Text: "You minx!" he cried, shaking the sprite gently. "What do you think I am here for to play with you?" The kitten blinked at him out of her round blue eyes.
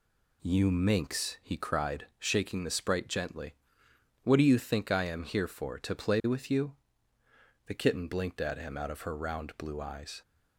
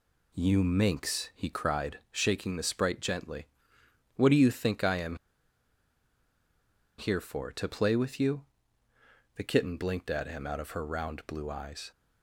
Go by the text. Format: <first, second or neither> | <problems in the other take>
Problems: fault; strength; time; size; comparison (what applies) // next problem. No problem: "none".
first | pauses between "am" and "here"; strong; at 5.1 s; 1.8 s long